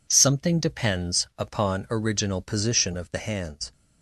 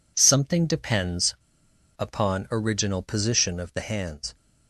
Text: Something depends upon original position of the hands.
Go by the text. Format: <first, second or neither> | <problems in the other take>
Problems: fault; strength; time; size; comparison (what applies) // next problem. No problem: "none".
first | pauses between "depends" and "upon"; noticeable; at 1.3 s; 0.63 s long